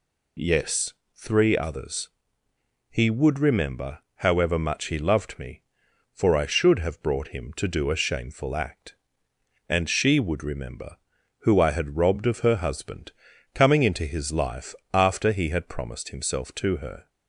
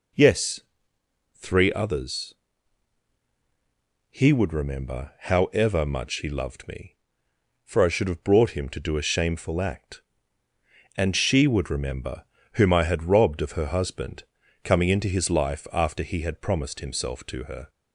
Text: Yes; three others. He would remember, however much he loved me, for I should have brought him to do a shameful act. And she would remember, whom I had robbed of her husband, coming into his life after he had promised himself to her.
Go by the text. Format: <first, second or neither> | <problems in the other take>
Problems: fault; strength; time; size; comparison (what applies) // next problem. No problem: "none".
second | says "who" for "whom"; at 11.3 s // pauses between "life" and "after"; slight; at 14.7 s; 0.18 s long